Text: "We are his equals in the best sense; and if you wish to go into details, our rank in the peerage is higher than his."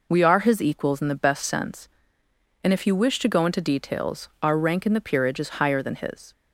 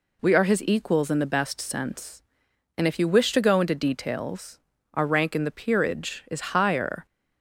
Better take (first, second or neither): first